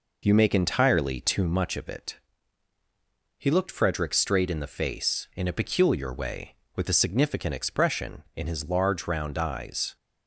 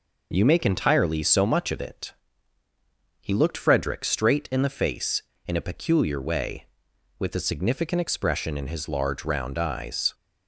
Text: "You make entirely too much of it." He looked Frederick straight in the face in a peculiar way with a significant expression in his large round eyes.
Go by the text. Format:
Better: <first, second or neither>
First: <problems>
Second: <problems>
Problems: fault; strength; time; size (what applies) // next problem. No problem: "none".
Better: first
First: none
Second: says "so" for "too"; at 1.2 s